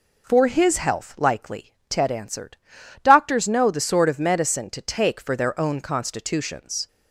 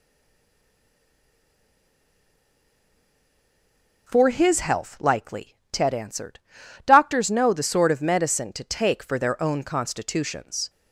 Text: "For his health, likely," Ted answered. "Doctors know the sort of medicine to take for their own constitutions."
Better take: first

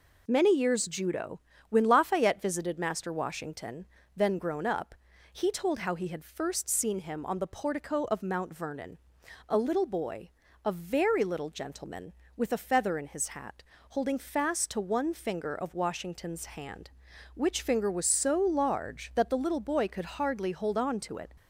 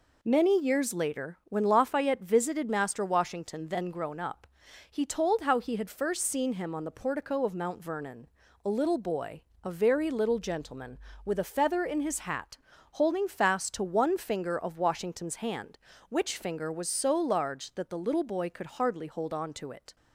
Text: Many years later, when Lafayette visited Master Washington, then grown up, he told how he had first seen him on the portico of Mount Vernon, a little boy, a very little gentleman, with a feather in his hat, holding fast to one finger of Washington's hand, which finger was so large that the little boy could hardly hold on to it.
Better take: second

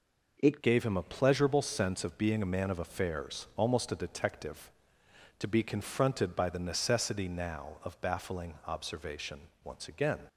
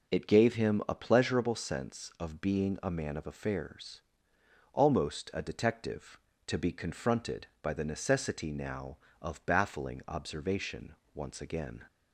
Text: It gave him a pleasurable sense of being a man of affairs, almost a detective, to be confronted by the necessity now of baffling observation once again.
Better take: second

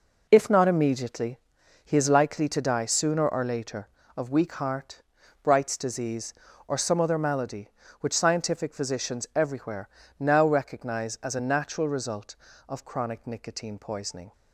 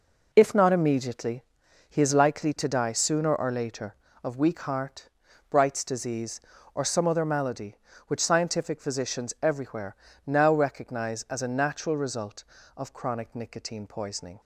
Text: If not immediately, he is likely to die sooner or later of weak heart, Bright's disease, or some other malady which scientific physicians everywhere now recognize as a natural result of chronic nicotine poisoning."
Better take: neither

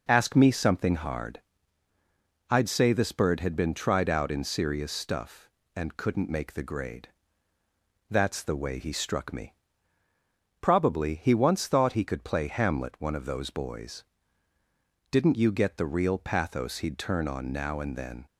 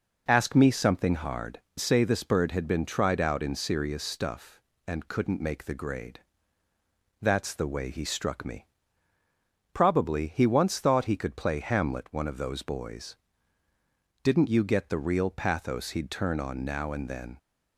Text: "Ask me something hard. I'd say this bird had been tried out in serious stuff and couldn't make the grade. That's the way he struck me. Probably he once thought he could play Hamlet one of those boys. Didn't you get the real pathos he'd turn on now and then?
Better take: first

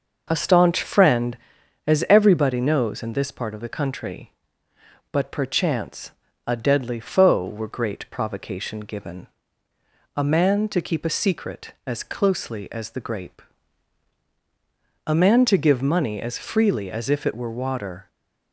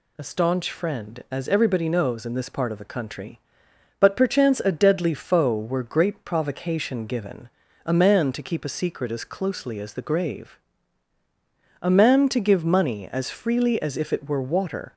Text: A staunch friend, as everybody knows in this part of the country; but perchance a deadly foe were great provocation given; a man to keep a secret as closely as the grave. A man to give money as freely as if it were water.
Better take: second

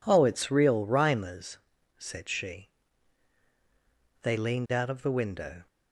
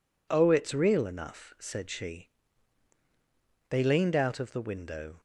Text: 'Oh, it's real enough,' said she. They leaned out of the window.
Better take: second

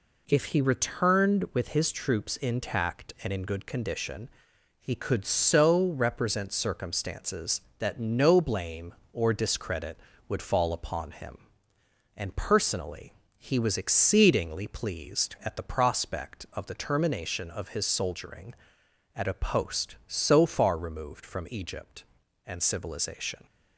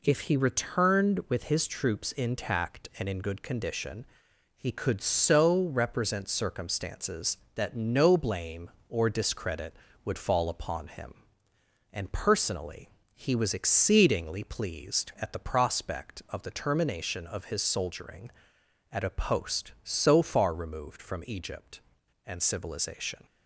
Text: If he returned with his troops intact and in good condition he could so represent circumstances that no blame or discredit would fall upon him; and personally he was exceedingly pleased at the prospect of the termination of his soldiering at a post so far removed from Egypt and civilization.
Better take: neither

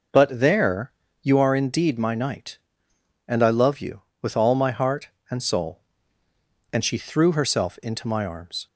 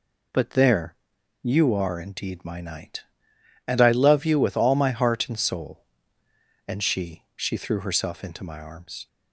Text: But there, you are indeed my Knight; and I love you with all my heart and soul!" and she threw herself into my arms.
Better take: first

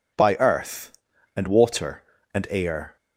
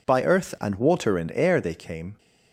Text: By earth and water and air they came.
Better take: second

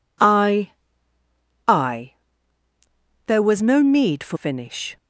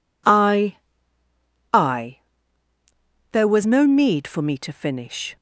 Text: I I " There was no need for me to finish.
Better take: second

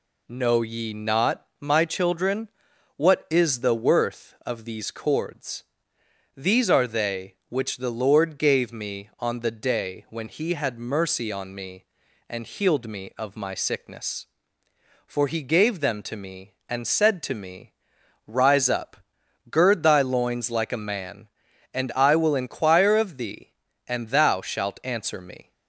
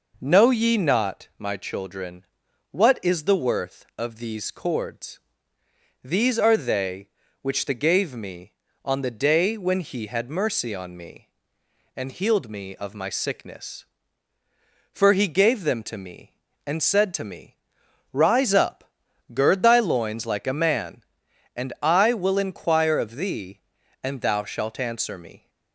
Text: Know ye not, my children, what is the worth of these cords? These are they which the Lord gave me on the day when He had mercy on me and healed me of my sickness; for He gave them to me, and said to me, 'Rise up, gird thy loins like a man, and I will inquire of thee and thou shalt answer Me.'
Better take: first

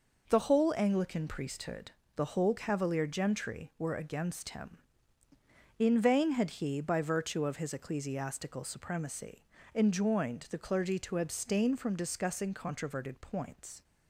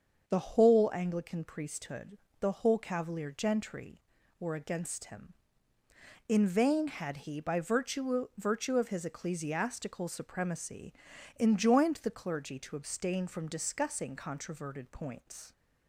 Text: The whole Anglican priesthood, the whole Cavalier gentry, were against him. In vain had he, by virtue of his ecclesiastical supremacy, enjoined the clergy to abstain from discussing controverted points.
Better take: first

